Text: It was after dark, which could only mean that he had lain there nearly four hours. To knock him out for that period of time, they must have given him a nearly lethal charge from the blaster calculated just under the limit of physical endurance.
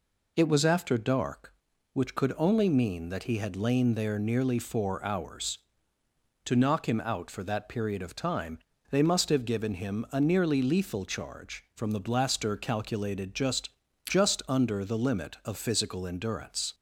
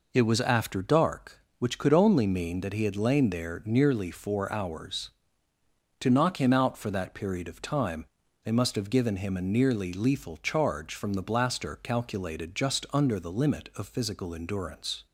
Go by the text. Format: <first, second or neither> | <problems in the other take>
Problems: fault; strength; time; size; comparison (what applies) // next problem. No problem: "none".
second | says "just" twice; at 14.0 s